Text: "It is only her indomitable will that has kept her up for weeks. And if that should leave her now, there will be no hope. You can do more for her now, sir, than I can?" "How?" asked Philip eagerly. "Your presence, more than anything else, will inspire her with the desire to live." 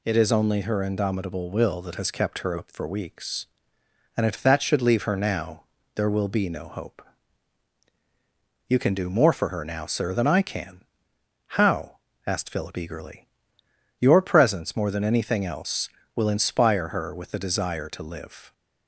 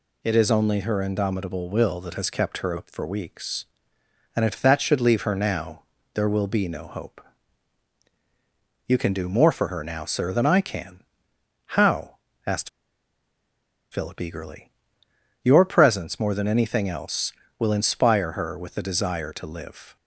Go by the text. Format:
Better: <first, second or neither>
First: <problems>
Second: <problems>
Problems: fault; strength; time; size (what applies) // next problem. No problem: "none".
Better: first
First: none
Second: pauses between "asked" and "Philip"; at 12.6 s; 1.2 s long